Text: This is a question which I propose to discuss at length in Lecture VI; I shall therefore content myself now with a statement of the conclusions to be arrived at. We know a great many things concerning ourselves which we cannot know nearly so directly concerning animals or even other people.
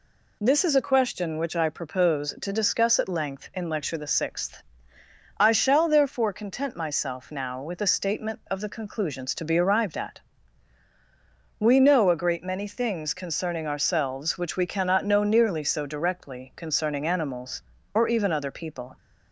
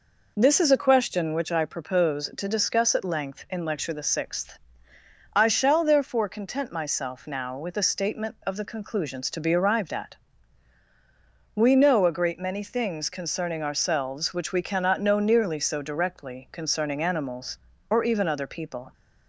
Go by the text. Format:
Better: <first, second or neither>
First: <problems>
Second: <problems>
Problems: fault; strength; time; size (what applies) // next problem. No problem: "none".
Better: first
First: none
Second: starts louder than the rest; noticeable; until 1.5 s; 4.5 dB